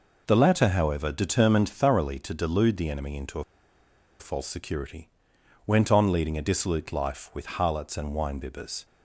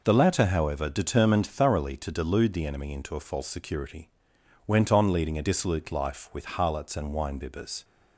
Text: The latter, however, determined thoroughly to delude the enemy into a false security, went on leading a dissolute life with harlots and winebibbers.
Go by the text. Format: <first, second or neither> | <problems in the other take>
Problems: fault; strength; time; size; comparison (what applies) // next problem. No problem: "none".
second | pauses between "a" and "false"; noticeable; at 3.4 s; 0.76 s long